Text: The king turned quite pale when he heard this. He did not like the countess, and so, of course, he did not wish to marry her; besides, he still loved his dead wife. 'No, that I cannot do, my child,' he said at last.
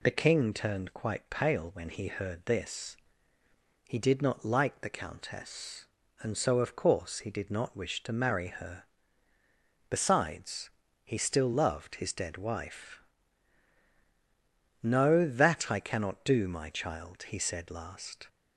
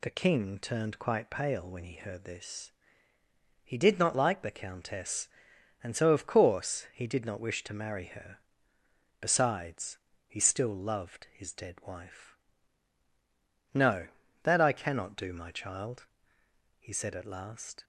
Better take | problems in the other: second | skips "at"; at 17.6 s

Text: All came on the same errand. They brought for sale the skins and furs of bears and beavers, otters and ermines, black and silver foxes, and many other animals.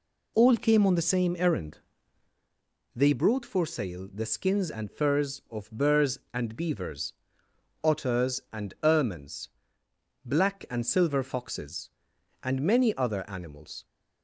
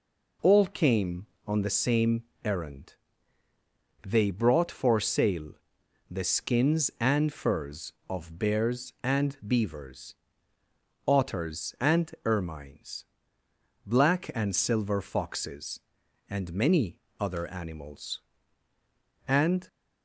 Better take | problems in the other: first | pauses between "same" and "errand"; slight; at 2.2 s; 0.22 s long // pauses between "sale" and "the"; noticeable; at 5.5 s; 0.56 s long // pauses between "many" and "other"; slight; at 16.9 s; 0.22 s long // goes on to say "And"; slight; from 19.2 s on; 0.40 s long

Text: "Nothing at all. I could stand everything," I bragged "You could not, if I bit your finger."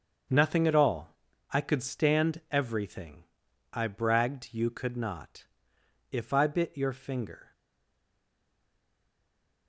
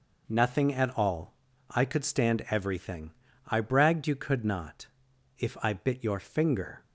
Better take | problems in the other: second | starts louder than the rest; until 1.6 s; 6.5 dB // stays silent after the last word; from 7.5 s on; 2.1 s long

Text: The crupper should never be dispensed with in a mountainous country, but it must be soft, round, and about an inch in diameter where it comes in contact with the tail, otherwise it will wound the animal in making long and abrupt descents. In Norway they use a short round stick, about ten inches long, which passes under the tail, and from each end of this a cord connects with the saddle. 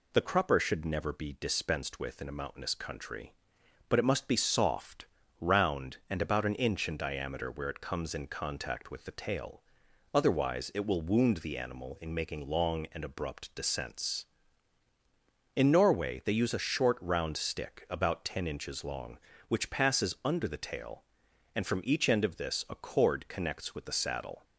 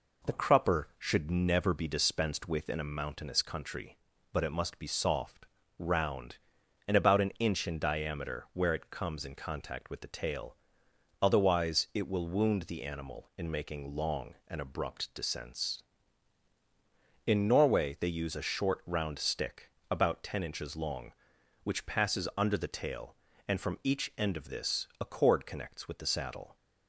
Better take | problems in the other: neither | none

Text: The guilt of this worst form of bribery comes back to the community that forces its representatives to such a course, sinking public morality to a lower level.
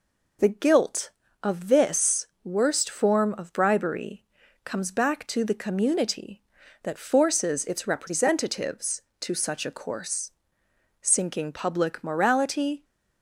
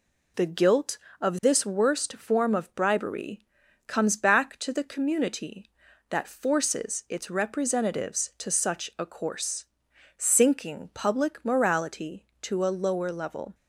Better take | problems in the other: second | pauses between "this" and "worst"; slight; at 2.2 s; 0.18 s long // pauses between "bribery" and "comes"; at 4.2 s; 0.40 s long; also in the second // stops before "to a lower level"; at 12.8 s

